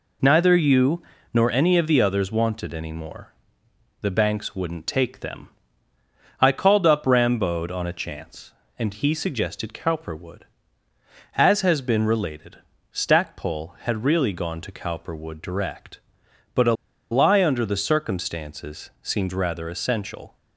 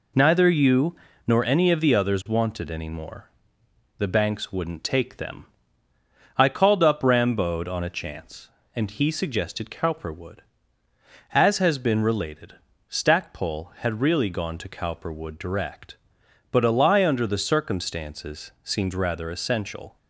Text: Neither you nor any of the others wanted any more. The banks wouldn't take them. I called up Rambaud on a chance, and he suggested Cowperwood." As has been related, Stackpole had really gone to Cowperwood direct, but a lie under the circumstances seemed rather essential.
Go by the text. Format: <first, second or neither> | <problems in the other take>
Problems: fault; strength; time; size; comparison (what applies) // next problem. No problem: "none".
second | pauses between "you" and "nor"; slight; at 1.0 s; 0.32 s long; slight in the second // pauses between "a" and "lie"; at 16.7 s; 0.38 s long